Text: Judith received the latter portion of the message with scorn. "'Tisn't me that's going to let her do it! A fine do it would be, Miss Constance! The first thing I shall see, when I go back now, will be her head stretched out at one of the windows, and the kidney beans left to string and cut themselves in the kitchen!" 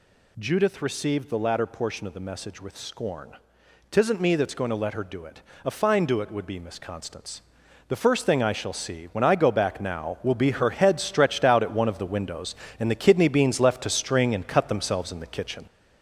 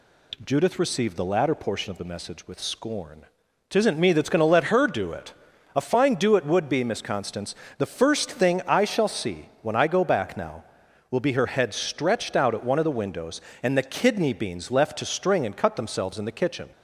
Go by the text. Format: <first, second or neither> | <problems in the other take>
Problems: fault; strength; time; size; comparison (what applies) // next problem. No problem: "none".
second | gets louder; noticeable; throughout; 5 dB